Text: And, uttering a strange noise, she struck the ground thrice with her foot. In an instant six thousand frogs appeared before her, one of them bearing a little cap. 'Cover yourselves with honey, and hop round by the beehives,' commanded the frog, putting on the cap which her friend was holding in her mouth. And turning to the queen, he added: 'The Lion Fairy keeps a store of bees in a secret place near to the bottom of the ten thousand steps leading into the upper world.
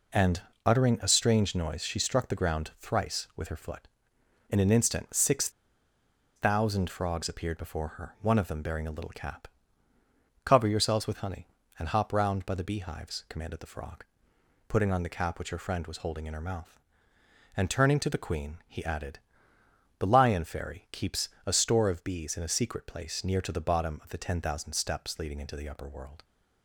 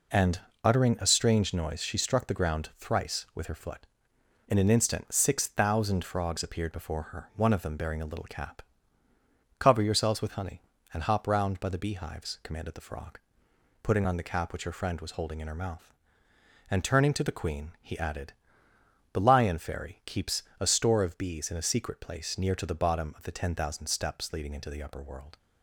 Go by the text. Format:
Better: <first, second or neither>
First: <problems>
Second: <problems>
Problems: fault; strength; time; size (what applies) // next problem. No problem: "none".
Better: second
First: pauses between "six" and "thousand"; noticeable; at 5.4 s; 0.86 s long // pauses between "keeps" and "a"; slight; at 21.2 s; 0.18 s long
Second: pauses between "keeps" and "a"; slight; at 20.4 s; 0.18 s long